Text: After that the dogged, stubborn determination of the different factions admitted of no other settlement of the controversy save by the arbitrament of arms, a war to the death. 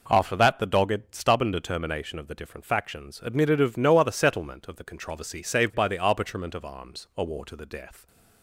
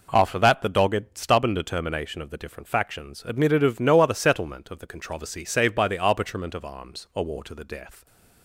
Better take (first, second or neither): neither